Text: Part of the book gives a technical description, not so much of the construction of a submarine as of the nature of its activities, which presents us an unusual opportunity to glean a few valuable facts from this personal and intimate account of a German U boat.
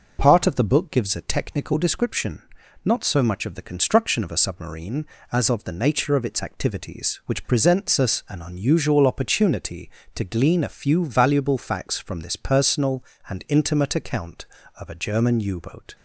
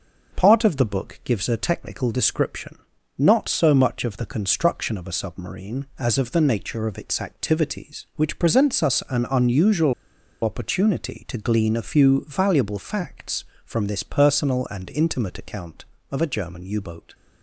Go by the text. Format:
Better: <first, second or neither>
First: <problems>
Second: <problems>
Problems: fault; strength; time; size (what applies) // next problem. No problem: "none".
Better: first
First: none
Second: pauses between "unusual" and "opportunity"; noticeable; at 9.9 s; 0.50 s long